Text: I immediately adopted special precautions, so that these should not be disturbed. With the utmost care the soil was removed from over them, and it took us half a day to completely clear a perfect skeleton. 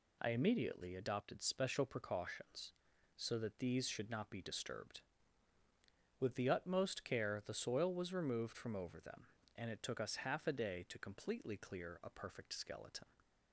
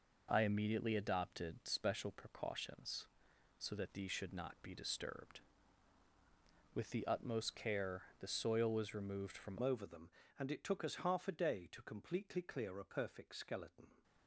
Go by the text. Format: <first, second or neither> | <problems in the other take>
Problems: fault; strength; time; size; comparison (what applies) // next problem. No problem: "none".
first | pauses between "care" and "the"; slight; at 8.0 s; 0.18 s long // changes voice at "over"; from 9.6 s on; 4.4 s long